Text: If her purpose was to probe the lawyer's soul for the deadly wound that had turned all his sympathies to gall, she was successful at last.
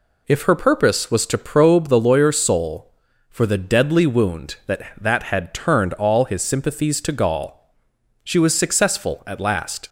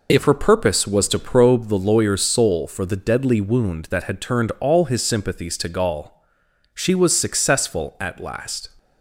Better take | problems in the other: second | says "that" twice; at 4.9 s

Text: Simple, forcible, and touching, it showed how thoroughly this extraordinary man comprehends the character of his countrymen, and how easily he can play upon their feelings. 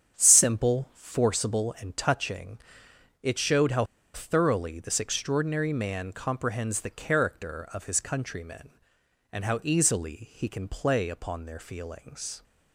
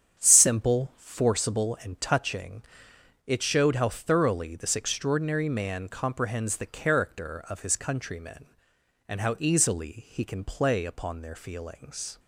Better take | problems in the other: second | starts louder than the rest; strong; until 1.2 s; 8 dB; strong in the second // pauses between "how" and "thoroughly"; slight; at 3.8 s; 0.31 s long

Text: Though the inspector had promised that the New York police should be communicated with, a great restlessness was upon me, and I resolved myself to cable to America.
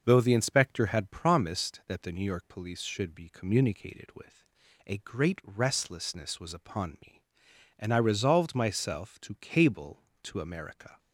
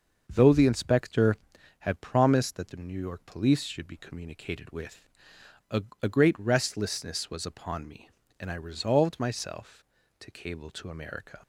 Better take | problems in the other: first | starts louder than the rest; until 1.2 s; 6.5 dB; noticeable in the first // says "a" twice; at 6.0 s

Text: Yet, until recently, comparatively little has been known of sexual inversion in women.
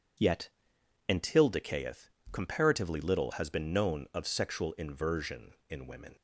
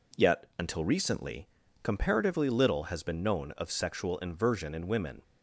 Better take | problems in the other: second | says "decayeth" for "recently"; at 1.4 s

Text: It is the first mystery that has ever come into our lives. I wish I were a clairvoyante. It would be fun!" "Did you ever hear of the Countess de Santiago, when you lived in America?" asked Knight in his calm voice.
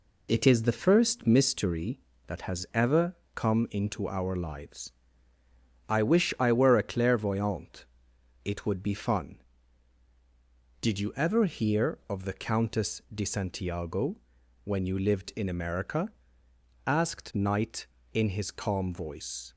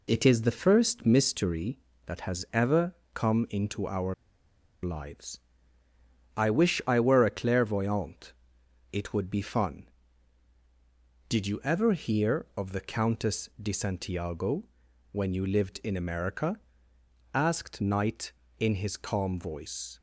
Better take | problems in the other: first | pauses between "ever" and "come"; slight; at 2.9 s; 0.18 s long; slight in the first // pauses between "our" and "lives"; noticeable; at 4.1 s; 0.69 s long

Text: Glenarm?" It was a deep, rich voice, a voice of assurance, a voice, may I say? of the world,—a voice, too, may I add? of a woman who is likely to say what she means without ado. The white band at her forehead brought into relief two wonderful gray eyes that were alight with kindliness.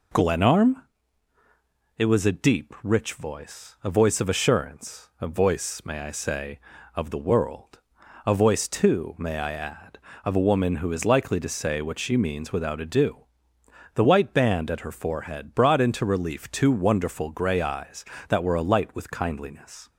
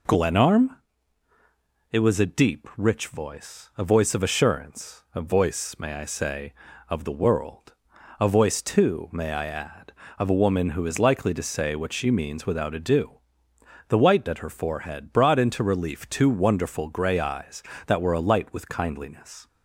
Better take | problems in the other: first | skips "band"; at 14.2 s

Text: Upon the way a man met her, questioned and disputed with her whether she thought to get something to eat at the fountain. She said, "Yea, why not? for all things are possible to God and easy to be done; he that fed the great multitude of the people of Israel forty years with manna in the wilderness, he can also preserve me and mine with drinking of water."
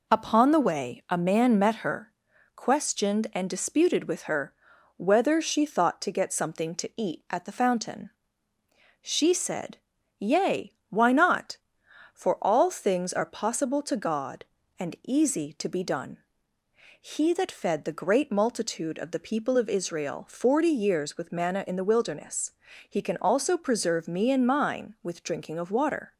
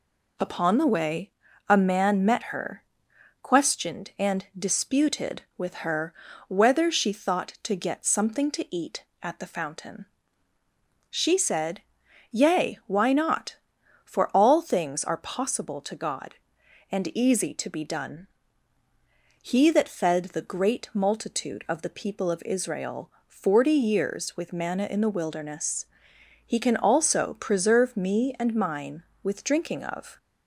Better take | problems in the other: first | pauses between "way" and "a"; at 1.3 s; 0.38 s long // pauses between "her" and "whether"; slight; at 6.1 s; 0.36 s long; also in the first // pauses between "Israel" and "forty"; slight; at 23.1 s; 0.16 s long // stops before "water"; at 30.1 s

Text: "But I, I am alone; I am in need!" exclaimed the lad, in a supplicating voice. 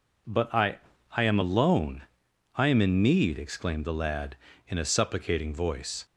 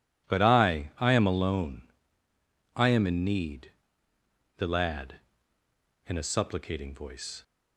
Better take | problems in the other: first | skips "exclaimed"; at 4.1 s

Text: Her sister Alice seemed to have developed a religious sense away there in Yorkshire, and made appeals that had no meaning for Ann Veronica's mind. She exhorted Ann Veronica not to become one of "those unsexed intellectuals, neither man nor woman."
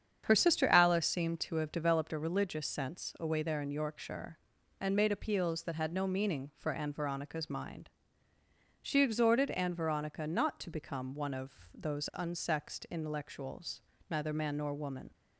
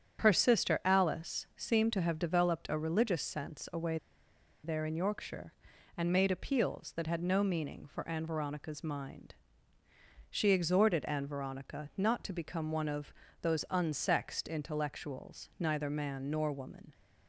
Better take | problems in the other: first | starts louder than the rest; strong; until 1.2 s; 8.5 dB; strong in the first // pauses between "away" and "there"; noticeable; at 3.9 s; 0.67 s long // pauses between "of" and "those"; slight; at 13.1 s; 0.26 s long

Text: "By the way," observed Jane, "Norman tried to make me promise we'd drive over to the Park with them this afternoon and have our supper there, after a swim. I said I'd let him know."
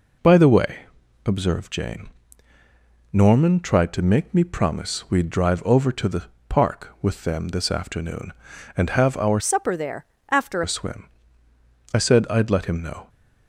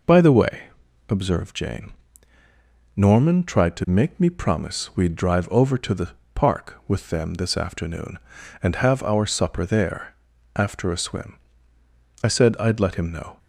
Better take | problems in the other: second | pauses between "the" and "Park"; slight; at 6.2 s; 0.24 s long; slight in the second // changes voice from "supper" to "after"; from 9.3 to 10.6 s; 1.3 s long

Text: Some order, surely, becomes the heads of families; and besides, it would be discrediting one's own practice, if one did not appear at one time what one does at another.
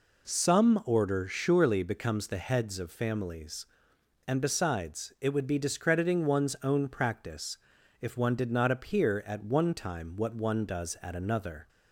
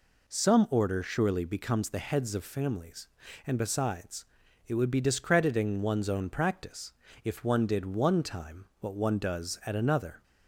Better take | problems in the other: first | skips "not appear at"; at 7.8 s // pauses between "time" and "what"; slight; at 8.6 s; 0.16 s long

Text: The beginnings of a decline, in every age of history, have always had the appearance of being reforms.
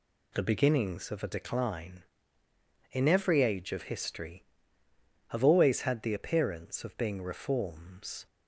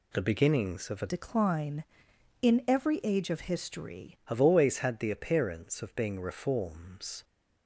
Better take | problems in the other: first | changes voice from "decline" to "history"; from 1.0 to 4.1 s; 3.1 s long

